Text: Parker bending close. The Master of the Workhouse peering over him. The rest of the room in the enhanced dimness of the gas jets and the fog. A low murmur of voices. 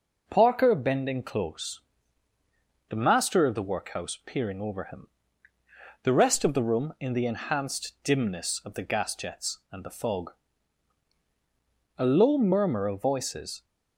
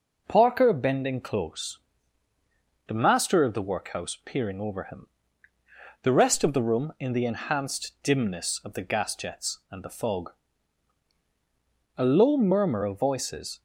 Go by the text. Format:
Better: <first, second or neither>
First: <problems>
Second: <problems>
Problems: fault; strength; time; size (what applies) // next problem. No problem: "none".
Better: neither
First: none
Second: none